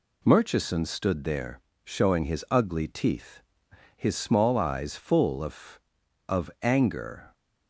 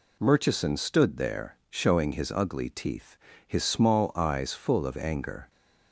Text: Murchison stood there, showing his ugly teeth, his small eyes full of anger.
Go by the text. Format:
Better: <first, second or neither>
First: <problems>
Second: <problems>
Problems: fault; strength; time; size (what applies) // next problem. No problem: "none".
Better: second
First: says "of" twice; at 6.2 s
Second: none